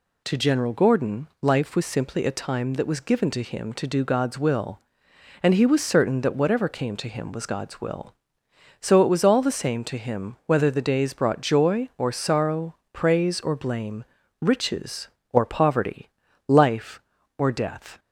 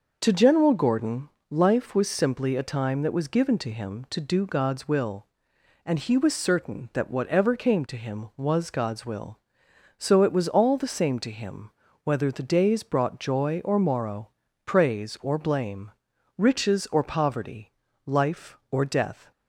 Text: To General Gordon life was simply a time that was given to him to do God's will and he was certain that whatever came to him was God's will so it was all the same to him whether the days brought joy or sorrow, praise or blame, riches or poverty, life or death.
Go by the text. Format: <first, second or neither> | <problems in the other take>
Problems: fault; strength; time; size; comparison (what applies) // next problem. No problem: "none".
first | pauses between "Gordon" and "life"; slight; at 1.2 s; 0.20 s long // pauses between "him" and "whether"; slight; at 11.7 s; 0.32 s long // says "morrow" for "sorrow"; at 13.7 s